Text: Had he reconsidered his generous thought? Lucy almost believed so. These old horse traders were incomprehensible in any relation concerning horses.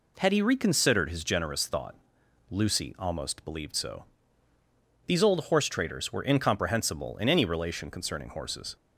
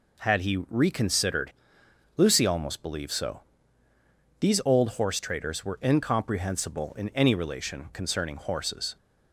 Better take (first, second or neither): first